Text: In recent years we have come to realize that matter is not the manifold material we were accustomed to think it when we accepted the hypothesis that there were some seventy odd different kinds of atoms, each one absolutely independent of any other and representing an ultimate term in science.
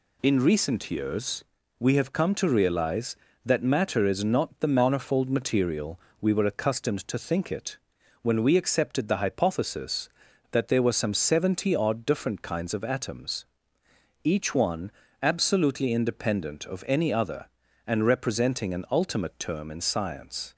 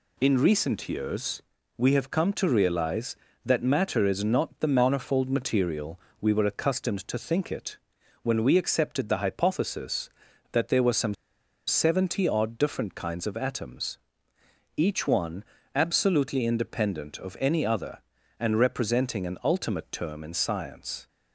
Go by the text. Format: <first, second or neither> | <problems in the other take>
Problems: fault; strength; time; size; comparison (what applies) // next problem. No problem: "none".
first | pauses between "years" and "we"; slight; at 1.4 s; 0.34 s long; slight in the first // pauses between "material" and "we"; slight; at 5.9 s; 0.20 s long; slight in the first // pauses between "it" and "when"; noticeable; at 7.7 s; 0.46 s long; also in the first // pauses between "some" and "seventy"; noticeable; at 11.1 s; 0.53 s long // pauses between "one" and "absolutely"; slight; at 15.4 s; 0.30 s long; slight in the first